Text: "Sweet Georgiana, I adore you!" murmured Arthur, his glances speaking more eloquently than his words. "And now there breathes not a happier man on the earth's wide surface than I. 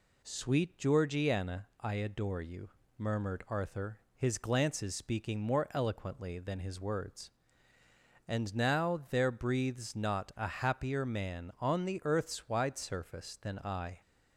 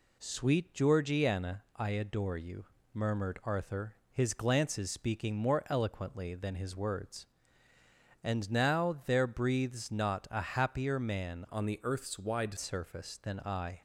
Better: first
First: none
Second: changes voice from "on" to "wide"; from 11.4 to 12.5 s; 1.1 s long

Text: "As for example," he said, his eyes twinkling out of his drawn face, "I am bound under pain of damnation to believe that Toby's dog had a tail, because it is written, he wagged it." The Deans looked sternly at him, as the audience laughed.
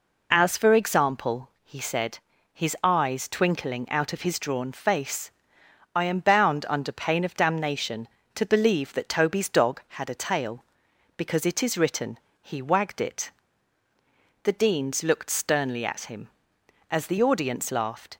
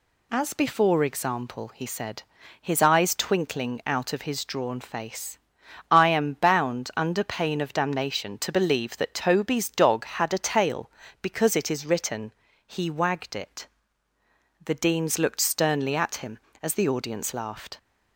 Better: first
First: none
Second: says "before" for "for"; at 0.5 s

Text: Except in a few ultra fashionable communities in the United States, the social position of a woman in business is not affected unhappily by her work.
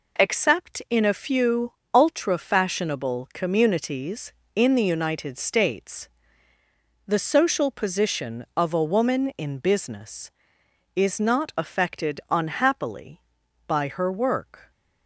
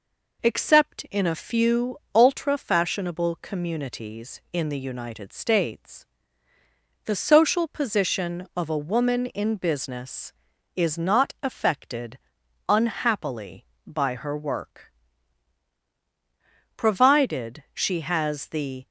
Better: first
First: pauses between "few" and "ultra"; slight; at 1.7 s; 0.20 s long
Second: pauses between "few" and "ultra"; slight; at 1.9 s; 0.18 s long // pauses between "affected" and "unhappily"; noticeable; at 12.1 s; 0.52 s long // goes on to say "Provided she has the"; strong; from 17.0 s on; 1.8 s long

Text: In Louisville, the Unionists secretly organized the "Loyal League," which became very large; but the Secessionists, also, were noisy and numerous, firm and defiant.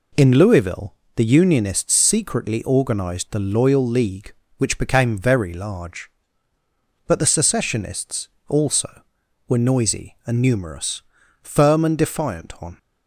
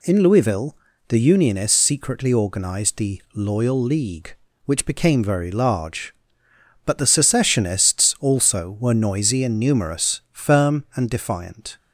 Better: second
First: goes on to say "On"; slight; from 12.6 s on; 0.16 s long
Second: none

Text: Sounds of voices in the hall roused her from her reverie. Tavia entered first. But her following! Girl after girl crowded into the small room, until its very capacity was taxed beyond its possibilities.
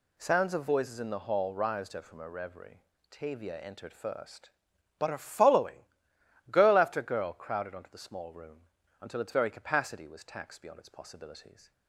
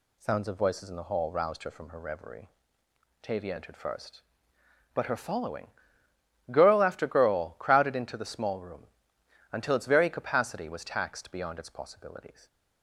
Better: second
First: says "onto" for "into"; at 7.7 s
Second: none

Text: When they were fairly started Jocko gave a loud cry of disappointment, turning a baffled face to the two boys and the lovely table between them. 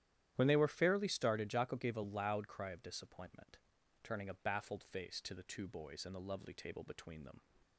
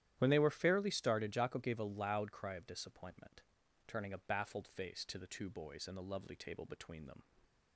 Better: neither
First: starts louder than the rest; strong; until 1.3 s; 11.5 dB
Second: starts louder than the rest; strong; until 1.1 s; 11.5 dB

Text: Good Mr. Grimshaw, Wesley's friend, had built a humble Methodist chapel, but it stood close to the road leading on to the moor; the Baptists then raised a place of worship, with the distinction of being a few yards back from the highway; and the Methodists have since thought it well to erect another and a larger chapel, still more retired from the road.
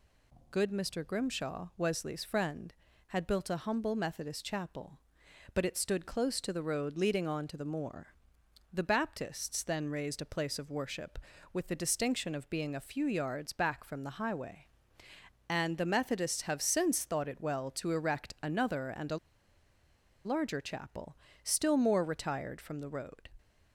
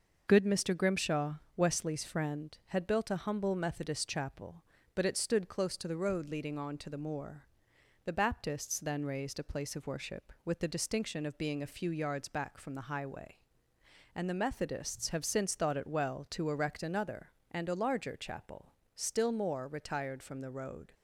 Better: second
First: pauses between "a" and "larger"; at 19.1 s; 1.0 s long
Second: none

